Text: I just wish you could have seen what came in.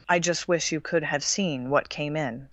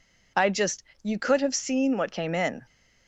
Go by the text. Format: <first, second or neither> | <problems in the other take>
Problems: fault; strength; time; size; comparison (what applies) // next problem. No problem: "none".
first | skips "wish"; at 0.9 s